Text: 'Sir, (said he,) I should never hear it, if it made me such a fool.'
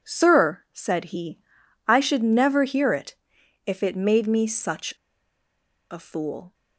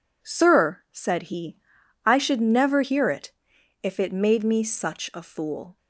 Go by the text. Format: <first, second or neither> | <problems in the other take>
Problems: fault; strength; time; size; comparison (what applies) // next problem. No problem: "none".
second | pauses between "such" and "a"; at 4.9 s; 0.99 s long